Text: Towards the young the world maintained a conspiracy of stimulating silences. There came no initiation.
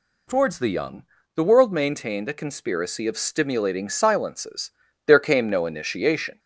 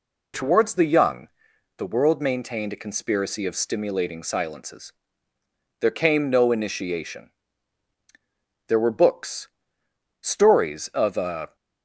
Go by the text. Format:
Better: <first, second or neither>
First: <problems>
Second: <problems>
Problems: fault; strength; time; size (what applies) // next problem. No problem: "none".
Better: first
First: pauses between "young" and "the"; slight; at 1.0 s; 0.34 s long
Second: pauses between "young" and "the"; noticeable; at 1.2 s; 0.48 s long // goes on to say "There were books stories of a"; strong; from 8.6 s on; 2.8 s long